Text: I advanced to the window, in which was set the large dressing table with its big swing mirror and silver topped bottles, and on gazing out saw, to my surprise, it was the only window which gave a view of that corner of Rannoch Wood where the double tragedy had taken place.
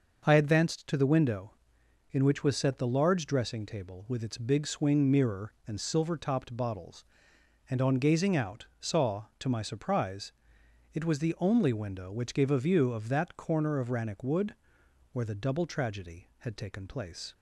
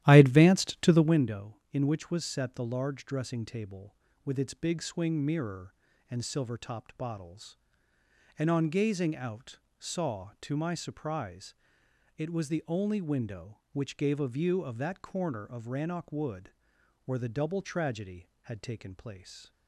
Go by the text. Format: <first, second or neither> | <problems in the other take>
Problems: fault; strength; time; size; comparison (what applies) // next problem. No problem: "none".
first | starts louder than the rest; strong; until 1.3 s; 13 dB // pauses between "out" and "saw"; slight; at 9.5 s; 0.18 s long; slight in the first // pauses between "Wood" and "where"; noticeable; at 16.4 s; 0.56 s long; noticeable in the first